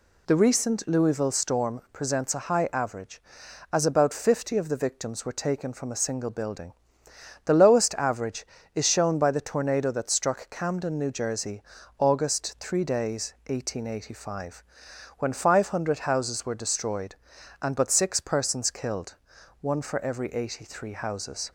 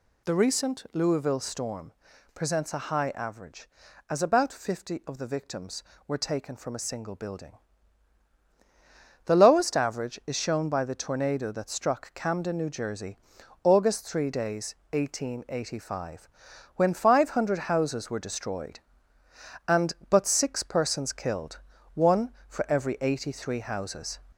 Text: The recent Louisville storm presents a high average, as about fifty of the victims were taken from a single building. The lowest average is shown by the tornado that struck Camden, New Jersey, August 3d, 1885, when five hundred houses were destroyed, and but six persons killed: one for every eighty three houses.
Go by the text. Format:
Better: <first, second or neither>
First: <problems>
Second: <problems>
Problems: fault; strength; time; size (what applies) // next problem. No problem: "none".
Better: first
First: none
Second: gets louder; slight; throughout; 2.5 dB // pauses between "storm" and "presents"; at 1.9 s; 0.42 s long